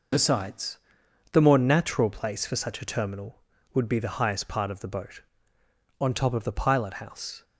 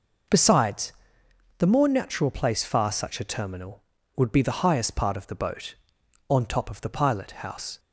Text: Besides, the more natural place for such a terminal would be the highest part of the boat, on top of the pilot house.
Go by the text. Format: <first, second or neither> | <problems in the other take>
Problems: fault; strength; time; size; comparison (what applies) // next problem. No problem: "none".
first | says "far" for "for"; at 2.6 s